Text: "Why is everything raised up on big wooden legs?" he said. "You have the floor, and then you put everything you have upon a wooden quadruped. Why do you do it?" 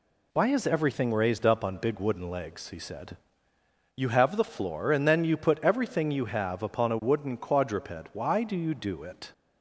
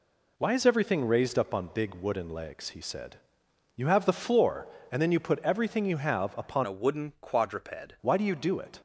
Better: first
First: none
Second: changes voice from "a" to "quadruped"; from 6.6 to 7.9 s; 1.3 s long

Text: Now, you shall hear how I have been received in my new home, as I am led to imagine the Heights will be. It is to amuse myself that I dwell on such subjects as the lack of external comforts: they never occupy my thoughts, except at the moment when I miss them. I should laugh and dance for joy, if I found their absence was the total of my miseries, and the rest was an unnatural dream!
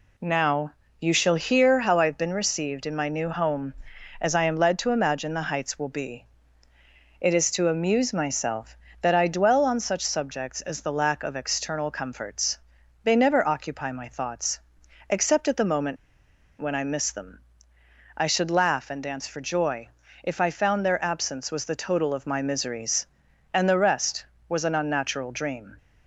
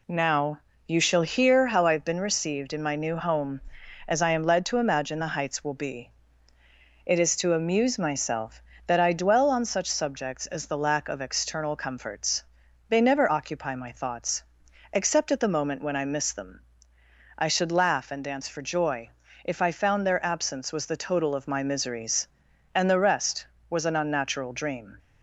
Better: second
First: pauses between "moment" and "when"; noticeable; at 15.9 s; 0.64 s long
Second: none

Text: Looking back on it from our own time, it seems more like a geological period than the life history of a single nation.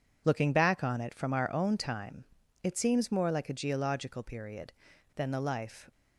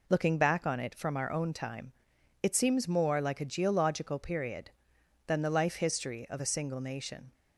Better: second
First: stops before "history of a single nation"; at 5.9 s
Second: none

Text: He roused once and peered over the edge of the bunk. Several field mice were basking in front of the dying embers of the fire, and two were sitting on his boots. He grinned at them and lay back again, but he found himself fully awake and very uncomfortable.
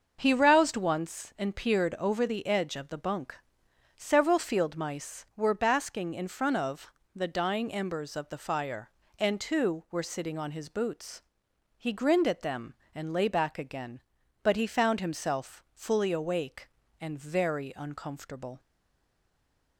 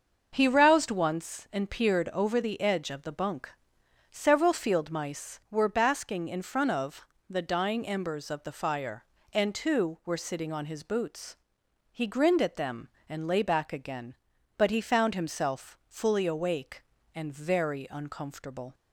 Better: second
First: starts louder than the rest; until 1.2 s; 6.5 dB // pauses between "of" and "the"; slight; at 6.9 s; 0.24 s long // stays silent after the last word; noticeable; from 18.5 s on; 1.2 s long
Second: starts louder than the rest; until 1.3 s; 6.5 dB // pauses between "of" and "the"; slight; at 7.0 s; 0.24 s long

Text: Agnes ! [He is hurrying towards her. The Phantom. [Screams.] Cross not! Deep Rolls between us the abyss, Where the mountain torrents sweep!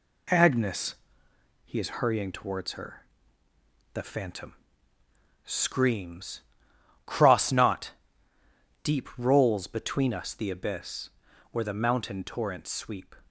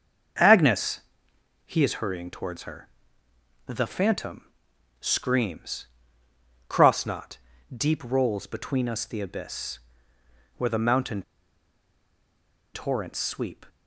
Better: first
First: none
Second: starts louder than the rest; until 2.0 s; 7 dB // pauses between "mountain" and "torrents"; strong; at 11.2 s; 1.5 s long

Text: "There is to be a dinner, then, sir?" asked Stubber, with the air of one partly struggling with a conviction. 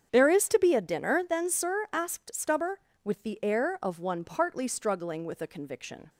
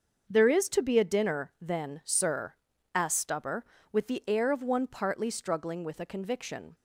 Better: neither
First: starts louder than the rest; strong; until 1.1 s; 8 dB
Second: starts louder than the rest; until 1.3 s; 6.5 dB

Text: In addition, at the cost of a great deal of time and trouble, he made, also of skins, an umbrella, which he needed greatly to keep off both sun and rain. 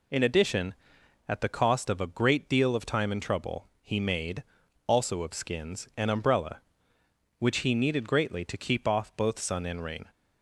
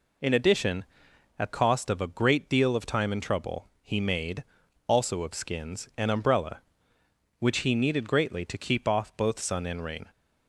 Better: first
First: none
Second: skips "the"; at 1.5 s

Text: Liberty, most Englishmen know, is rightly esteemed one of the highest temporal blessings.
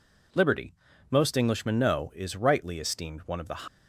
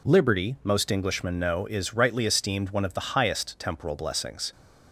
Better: second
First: stops before "highest temporal blessings"; at 3.6 s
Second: none

